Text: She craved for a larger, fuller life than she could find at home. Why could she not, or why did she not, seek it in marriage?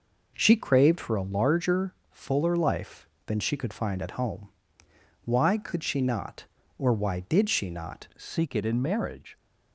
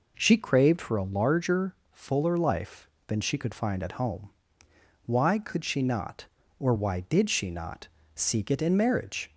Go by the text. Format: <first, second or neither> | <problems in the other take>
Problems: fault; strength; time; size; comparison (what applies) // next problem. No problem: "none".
second | changes voice at "seek"; from 8.1 s on; 1.2 s long